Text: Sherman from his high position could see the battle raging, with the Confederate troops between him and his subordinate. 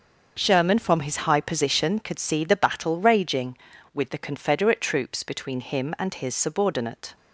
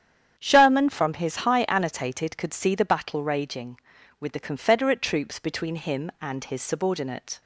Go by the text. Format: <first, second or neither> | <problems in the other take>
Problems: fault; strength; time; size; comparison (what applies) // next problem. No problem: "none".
first | starts louder than the rest; strong; until 1.3 s; 9 dB; also in the first // says "annotated" for "position"; at 1.6 s